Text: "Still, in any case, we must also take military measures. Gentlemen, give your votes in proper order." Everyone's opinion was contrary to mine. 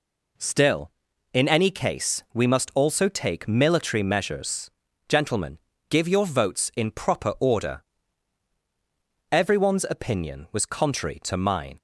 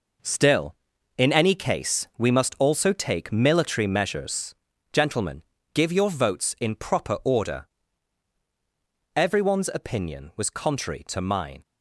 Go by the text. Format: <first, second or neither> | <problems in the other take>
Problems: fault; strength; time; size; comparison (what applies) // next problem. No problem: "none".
first | gets quieter; strong; throughout; 7.5 dB